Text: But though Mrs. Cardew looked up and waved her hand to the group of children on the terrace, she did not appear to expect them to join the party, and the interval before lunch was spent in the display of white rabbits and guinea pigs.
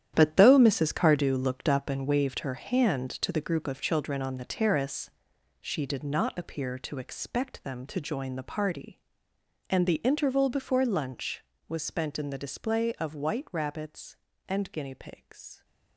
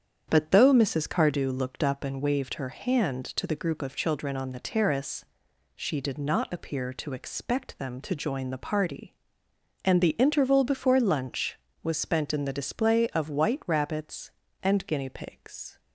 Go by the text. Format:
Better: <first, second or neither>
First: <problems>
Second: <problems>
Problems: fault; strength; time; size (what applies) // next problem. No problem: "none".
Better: second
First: gets quieter; strong; throughout; 11.5 dB // starts louder than the rest; strong; until 1.1 s; 10 dB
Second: starts louder than the rest; strong; until 1.3 s; 8 dB